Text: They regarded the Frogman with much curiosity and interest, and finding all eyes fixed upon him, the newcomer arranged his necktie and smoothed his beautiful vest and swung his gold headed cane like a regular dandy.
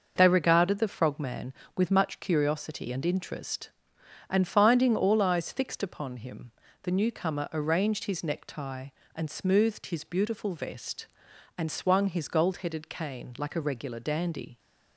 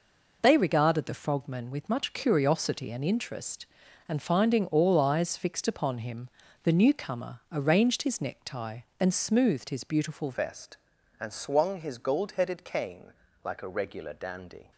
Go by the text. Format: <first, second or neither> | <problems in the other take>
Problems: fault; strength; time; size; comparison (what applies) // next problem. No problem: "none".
first | changes voice at "vest"; from 10.3 s on; 4.4 s long // pauses between "cane" and "like"; slight; at 13.1 s; 0.32 s long